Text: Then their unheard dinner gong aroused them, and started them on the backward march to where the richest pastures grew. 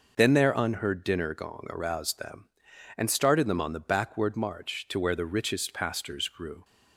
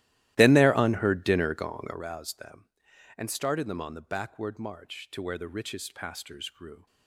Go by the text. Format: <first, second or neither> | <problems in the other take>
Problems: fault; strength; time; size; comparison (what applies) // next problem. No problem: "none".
first | starts louder than the rest; strong; until 2.0 s; 15.5 dB